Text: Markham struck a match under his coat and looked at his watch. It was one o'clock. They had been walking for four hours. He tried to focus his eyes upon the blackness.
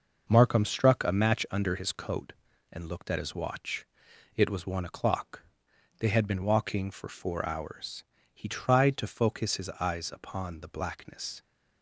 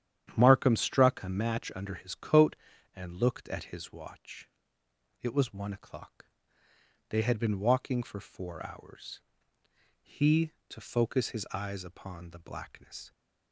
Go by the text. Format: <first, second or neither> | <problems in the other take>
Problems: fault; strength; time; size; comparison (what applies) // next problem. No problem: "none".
first | starts louder than the rest; strong; until 1.3 s; 10 dB // skips "tried"; at 10.5 s